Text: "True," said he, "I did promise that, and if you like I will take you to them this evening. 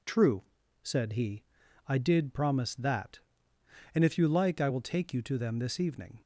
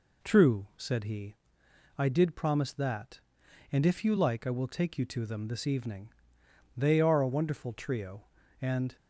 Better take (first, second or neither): first